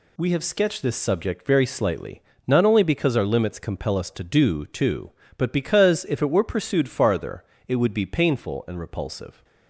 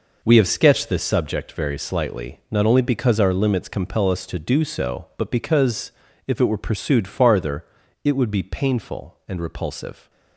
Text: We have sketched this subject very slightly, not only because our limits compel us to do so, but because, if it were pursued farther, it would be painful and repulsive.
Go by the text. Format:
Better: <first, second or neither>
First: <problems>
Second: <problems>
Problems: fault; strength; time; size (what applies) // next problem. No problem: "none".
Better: second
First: says "too" for "so"; at 4.6 s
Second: none